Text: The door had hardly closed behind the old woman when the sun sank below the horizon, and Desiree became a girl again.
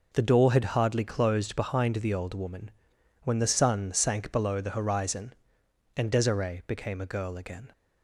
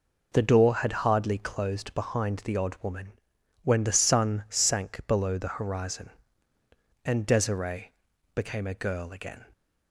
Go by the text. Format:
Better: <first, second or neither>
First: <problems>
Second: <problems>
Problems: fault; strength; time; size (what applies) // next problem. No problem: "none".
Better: first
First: pauses between "woman" and "when"; noticeable; at 2.7 s; 0.52 s long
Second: says "odd" for "old"; at 2.5 s // pauses between "woman" and "when"; noticeable; at 3.1 s; 0.52 s long // pauses between "Desiree" and "became"; at 7.9 s; 0.42 s long